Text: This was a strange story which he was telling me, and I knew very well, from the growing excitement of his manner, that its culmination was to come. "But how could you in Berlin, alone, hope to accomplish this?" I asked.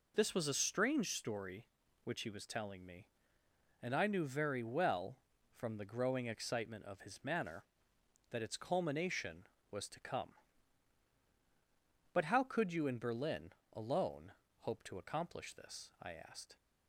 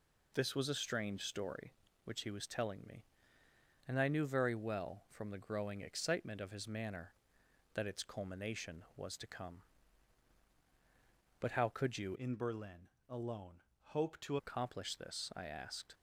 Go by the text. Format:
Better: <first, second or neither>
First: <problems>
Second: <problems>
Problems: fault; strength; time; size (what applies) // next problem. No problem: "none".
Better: first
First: none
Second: changes voice from "in" to "to"; from 12.1 to 14.3 s; 2.2 s long